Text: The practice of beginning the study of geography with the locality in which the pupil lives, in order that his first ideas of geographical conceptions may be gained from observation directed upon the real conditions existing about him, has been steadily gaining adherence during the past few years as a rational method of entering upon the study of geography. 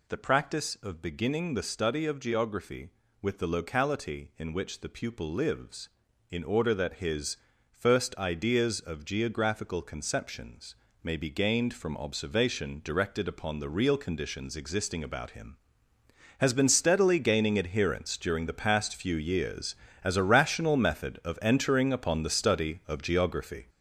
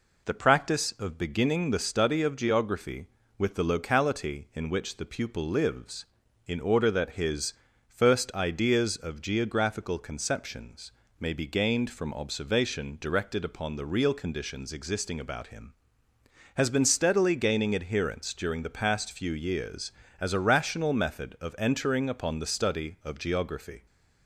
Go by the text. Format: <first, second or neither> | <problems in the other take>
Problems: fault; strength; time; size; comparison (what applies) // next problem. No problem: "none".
second | gets louder; noticeable; throughout; 6 dB // pauses between "his" and "first"; slight; at 7.3 s; 0.34 s long; slight in the second // pauses between "conceptions" and "may"; slight; at 10.7 s; 0.28 s long; slight in the second